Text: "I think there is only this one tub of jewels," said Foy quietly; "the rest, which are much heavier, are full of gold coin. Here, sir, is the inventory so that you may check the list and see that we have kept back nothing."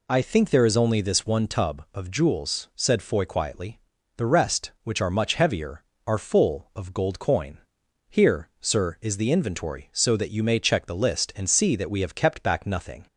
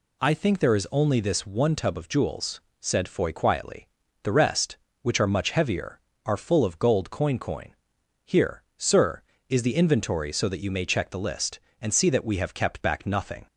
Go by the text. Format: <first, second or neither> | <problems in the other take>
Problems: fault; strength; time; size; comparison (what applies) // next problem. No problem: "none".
first | says "coin" twice; at 7.3 s